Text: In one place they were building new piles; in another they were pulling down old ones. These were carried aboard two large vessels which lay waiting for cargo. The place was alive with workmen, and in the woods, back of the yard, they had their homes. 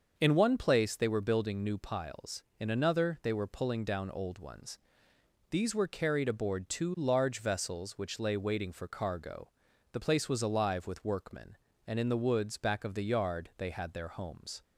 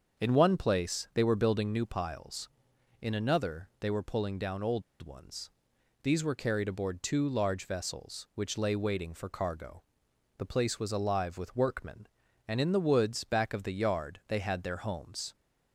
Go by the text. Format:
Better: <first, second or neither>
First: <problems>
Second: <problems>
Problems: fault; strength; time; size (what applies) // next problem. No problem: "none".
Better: first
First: starts louder than the rest; until 1.1 s; 6.5 dB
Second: starts louder than the rest; until 1.2 s; 6.5 dB // pauses between "old" and "ones"; slight; at 4.8 s; 0.20 s long